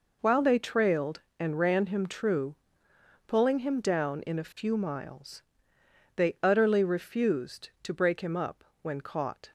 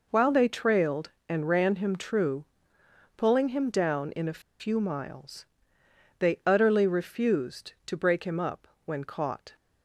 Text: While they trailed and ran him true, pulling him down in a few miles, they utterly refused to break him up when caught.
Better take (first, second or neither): first